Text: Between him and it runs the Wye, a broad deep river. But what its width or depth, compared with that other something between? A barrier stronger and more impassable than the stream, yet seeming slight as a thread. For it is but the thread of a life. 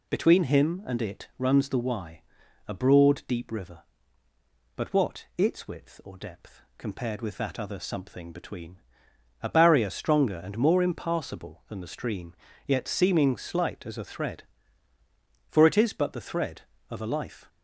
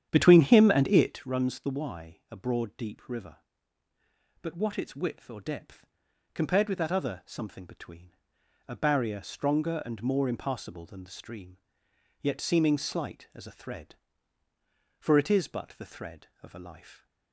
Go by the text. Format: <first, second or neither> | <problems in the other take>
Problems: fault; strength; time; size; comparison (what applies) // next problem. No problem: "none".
first | starts louder than the rest; strong; until 1.3 s; 9.5 dB